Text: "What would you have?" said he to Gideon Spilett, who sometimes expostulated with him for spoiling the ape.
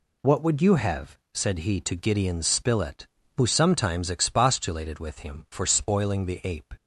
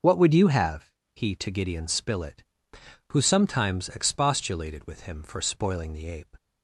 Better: first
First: none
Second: starts louder than the rest; noticeable; until 1.2 s; 6 dB // skips "said"; at 1.0 s

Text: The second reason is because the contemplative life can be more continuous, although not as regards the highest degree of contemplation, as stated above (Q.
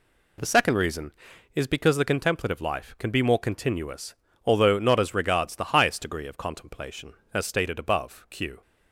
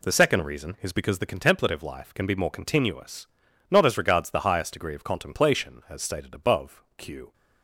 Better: first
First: none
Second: skips "although"; at 3.4 s

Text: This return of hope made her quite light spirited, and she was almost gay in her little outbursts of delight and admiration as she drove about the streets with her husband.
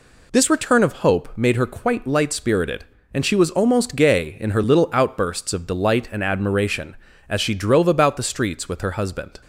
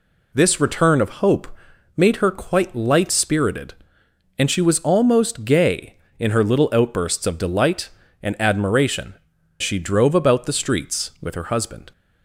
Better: first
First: none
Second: pauses between "hope" and "made"; noticeable; at 1.4 s; 0.50 s long // skips "as"; at 9.3 s

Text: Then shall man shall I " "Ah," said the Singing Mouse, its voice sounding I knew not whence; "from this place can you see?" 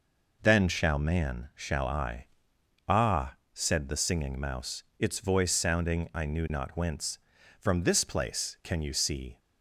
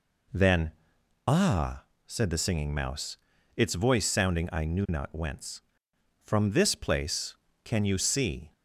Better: first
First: none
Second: skips "shall man shall I"; at 0.8 s

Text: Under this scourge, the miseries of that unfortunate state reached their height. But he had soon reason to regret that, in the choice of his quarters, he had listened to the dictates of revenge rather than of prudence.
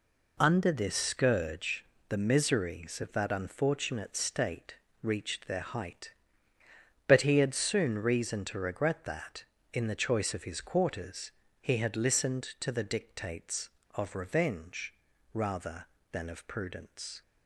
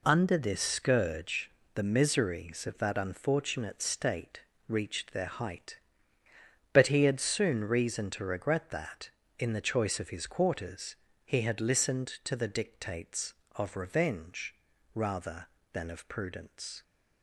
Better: neither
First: pauses between "state" and "reached"; slight; at 4.7 s; 0.28 s long // pauses between "revenge" and "rather"; at 14.9 s; 0.38 s long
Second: pauses between "state" and "reached"; slight; at 4.4 s; 0.28 s long // pauses between "revenge" and "rather"; at 14.5 s; 0.38 s long

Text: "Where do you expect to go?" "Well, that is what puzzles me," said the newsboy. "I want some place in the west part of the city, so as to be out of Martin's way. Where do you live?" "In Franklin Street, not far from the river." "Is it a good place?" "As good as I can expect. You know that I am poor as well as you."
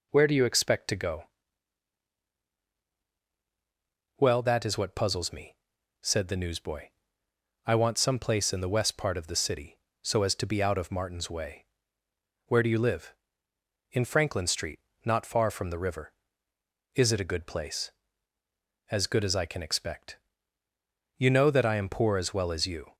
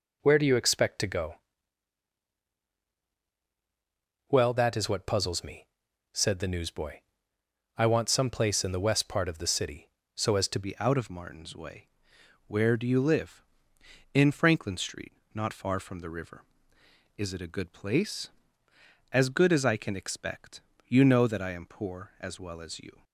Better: first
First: none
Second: changes voice at "be"; from 10.6 s on; 12.4 s long

